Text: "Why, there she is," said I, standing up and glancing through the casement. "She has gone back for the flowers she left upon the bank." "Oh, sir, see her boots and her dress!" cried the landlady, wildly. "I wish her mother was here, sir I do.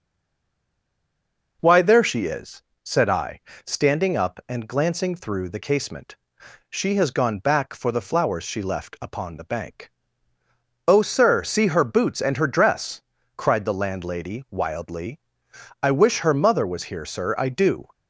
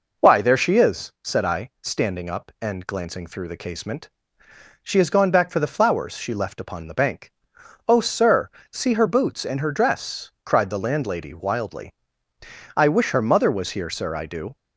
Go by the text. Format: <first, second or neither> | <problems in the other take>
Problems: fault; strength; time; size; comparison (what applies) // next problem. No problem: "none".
second | stays silent before the first word; noticeable; until 1.6 s; 1.6 s long